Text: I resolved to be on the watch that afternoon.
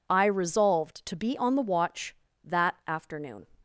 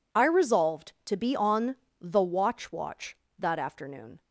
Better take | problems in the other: first | pauses between "on" and "the"; slight; at 1.7 s; 0.24 s long // says "watch" twice; at 2.7 s

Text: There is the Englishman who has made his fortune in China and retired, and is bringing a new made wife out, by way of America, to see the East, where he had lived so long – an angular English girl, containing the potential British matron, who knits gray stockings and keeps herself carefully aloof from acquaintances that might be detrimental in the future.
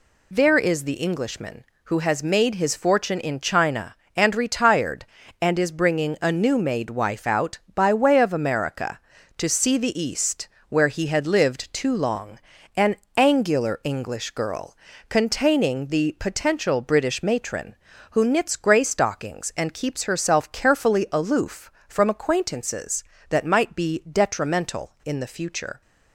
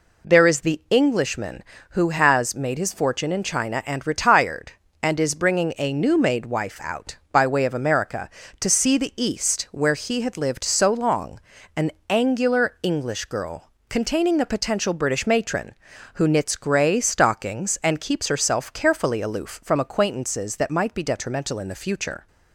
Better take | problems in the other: second | says "too" for "so"; at 11.7 s // pauses between "an" and "angular"; slight; at 12.9 s; 0.22 s long; slight in the second

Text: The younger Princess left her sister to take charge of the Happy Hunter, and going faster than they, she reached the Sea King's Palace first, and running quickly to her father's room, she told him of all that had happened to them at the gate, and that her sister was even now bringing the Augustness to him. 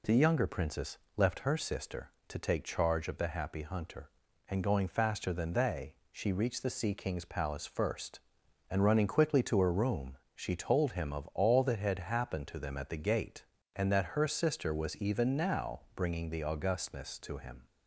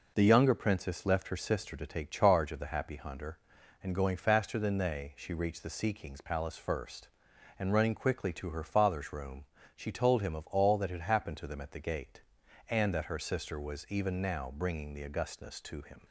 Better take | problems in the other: second | pauses between "Princess" and "left"; slight; at 0.9 s; 0.18 s long // skips "father's"; at 9.7 s // pauses between "now" and "bringing"; slight; at 15.7 s; 0.16 s long

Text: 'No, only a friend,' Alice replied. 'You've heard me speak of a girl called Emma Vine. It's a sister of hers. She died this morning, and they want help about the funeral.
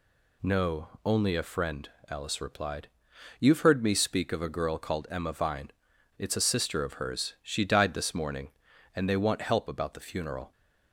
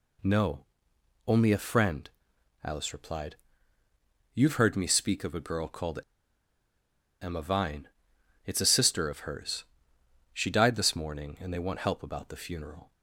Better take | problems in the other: first | pauses between "called" and "Emma"; at 5.9 s; 1.2 s long

